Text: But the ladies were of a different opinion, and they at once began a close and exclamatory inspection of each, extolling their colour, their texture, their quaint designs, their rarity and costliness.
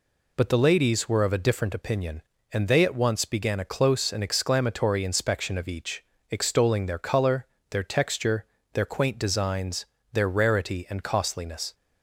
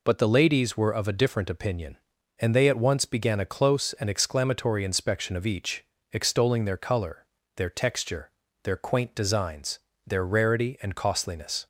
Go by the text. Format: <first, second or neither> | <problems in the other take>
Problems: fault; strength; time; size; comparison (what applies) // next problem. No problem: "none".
neither | none